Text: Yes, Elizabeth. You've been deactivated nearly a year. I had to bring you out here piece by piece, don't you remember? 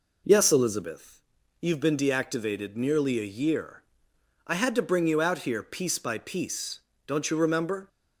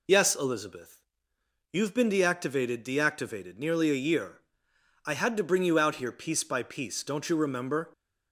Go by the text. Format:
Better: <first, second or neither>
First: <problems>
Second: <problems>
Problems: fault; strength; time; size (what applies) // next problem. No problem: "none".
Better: first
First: none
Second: says "deactivated" twice; at 2.8 s